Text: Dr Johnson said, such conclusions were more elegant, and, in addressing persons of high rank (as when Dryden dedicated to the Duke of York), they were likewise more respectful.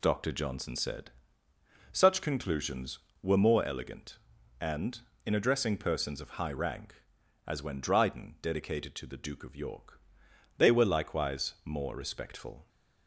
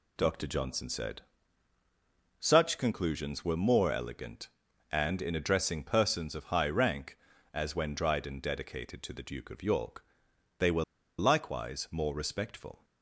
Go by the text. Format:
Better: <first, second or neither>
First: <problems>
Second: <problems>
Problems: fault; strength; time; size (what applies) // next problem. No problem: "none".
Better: first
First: none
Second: pauses between "were" and "likewise"; slight; at 10.8 s; 0.34 s long